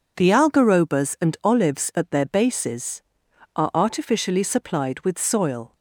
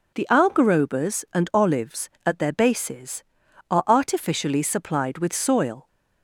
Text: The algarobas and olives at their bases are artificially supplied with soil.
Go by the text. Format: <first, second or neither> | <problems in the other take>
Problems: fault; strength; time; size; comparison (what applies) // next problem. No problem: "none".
neither | none